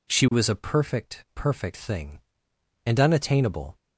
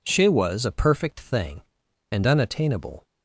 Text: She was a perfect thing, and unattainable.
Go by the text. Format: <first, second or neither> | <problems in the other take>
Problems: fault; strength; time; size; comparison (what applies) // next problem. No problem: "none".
second | says "perfect" twice; at 1.3 s